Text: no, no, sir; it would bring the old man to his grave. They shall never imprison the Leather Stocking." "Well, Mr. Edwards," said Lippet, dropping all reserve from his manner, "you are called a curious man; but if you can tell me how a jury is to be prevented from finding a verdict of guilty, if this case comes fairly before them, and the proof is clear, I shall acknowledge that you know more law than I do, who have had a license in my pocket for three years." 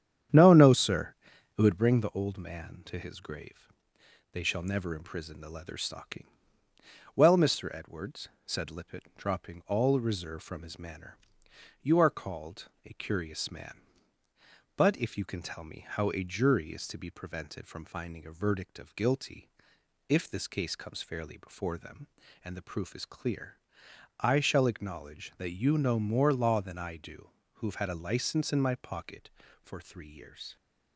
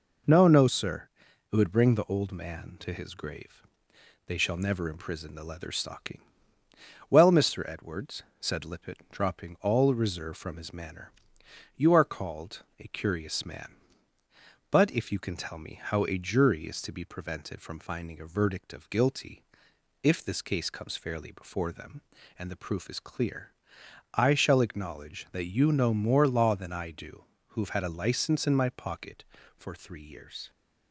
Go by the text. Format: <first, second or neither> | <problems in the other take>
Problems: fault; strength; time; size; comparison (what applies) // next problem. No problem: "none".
second | starts louder than the rest; strong; until 1.9 s; 9.5 dB // pauses between "called" and "a"; slight; at 12.6 s; 0.16 s long; slight in the second